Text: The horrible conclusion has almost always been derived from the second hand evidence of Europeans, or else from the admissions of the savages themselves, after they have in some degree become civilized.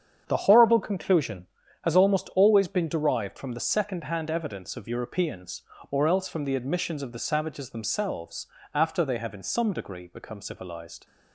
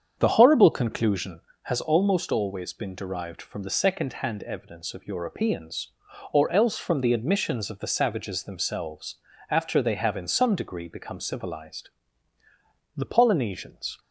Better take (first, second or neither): first